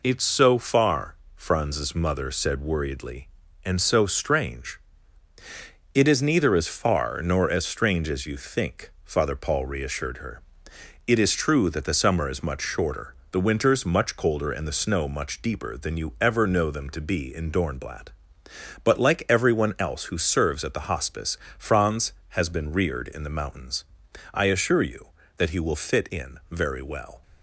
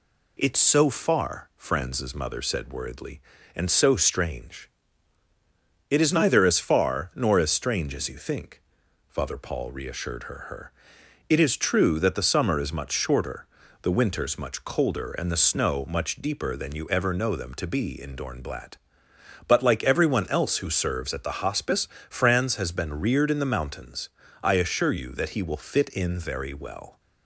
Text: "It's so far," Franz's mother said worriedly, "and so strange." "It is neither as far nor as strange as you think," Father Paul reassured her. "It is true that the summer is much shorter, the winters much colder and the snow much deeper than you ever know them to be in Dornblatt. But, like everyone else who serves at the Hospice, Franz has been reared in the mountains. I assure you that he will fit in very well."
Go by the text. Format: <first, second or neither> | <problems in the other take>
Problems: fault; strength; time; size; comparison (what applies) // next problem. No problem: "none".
first | says "her" twice; at 10.4 s